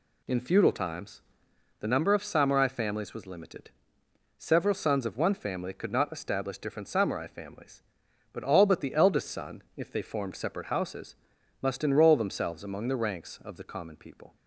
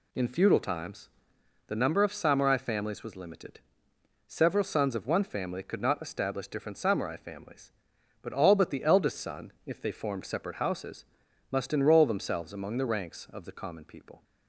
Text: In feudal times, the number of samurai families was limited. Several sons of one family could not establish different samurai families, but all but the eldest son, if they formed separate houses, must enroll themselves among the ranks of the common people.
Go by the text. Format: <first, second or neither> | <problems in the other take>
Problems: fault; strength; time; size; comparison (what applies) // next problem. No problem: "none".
neither | none